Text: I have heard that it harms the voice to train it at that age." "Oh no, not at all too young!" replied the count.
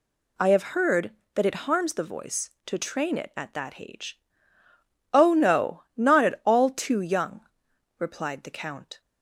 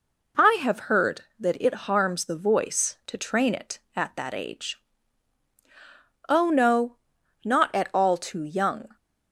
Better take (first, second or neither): first